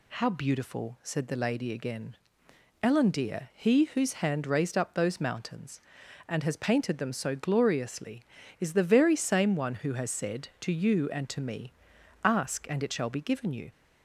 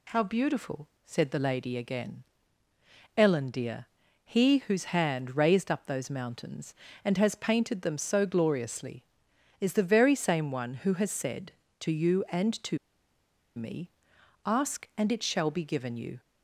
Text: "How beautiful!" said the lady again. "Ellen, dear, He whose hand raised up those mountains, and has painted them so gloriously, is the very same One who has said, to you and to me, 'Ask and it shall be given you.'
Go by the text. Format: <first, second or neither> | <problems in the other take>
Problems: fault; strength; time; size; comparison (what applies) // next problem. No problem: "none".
first | pauses between "to" and "me"; noticeable; at 12.7 s; 0.80 s long